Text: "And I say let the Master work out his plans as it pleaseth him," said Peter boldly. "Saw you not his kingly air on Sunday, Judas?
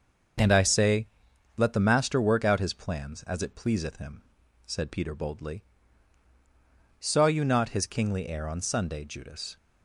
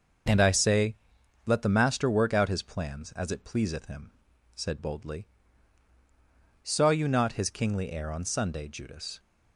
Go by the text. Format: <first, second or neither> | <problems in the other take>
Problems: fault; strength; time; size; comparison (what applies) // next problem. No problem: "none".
first | starts louder than the rest; noticeable; until 1.7 s; 6 dB; also in the first // pauses between "say" and "let"; noticeable; at 0.9 s; 0.48 s long; noticeable in the first // skips "Peter"; at 4.7 s